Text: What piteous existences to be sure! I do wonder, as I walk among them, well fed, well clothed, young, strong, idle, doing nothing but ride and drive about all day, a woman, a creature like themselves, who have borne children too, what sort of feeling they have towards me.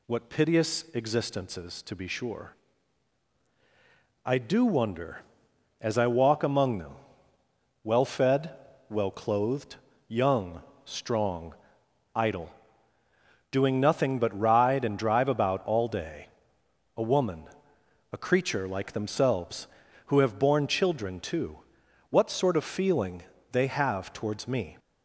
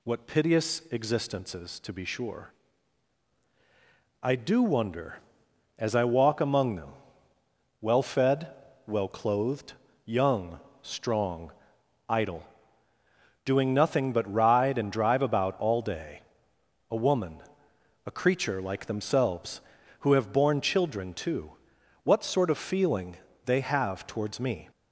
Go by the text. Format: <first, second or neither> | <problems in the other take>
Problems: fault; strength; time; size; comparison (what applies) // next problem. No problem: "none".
neither | pauses between "feeling" and "they"; slight; the same in both